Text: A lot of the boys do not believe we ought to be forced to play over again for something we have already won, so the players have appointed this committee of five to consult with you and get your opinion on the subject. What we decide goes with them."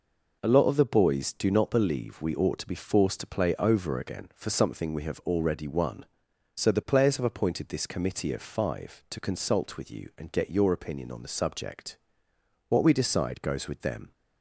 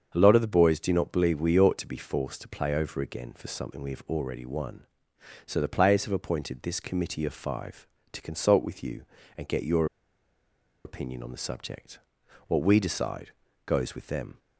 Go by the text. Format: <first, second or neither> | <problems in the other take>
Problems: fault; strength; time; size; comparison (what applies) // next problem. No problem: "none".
first | starts louder than the rest; until 1.1 s; 7 dB // pauses between "your" and "opinion"; at 9.8 s; 1.0 s long // pauses between "decide" and "goes"; slight; at 13.2 s; 0.36 s long